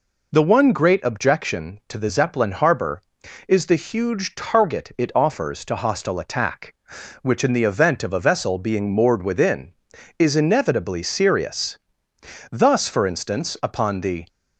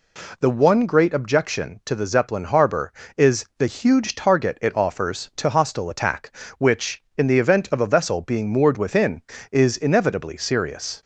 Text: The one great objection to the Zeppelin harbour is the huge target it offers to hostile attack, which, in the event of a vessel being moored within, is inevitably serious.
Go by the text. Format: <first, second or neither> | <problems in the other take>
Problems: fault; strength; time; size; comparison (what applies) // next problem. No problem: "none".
second | goes on to say "Thus for instance upon the"; strong; from 12.5 s on; 1.7 s long